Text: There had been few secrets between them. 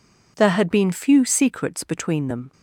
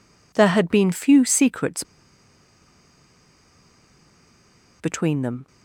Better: first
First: none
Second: pauses between "secrets" and "between"; strong; at 1.8 s; 2.9 s long

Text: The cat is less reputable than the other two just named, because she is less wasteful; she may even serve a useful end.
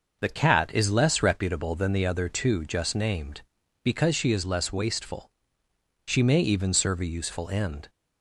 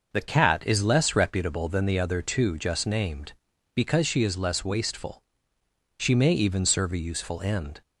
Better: neither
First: none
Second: none

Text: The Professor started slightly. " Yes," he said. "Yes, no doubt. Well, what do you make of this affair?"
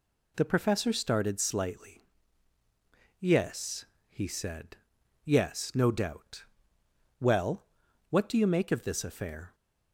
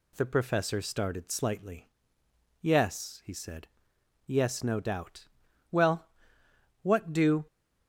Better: first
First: none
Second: stops before "you make of this affair"; at 7.4 s

